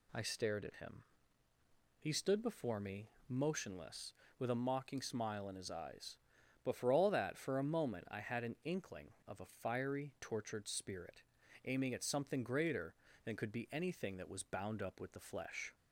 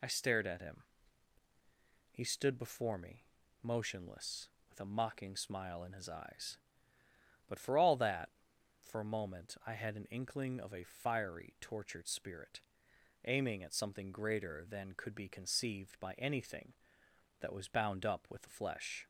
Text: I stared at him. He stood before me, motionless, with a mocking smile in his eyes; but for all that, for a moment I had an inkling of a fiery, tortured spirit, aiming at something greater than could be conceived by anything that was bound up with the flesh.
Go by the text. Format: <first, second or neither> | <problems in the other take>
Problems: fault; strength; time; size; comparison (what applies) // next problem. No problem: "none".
second | skips "conceived by"; at 13.6 s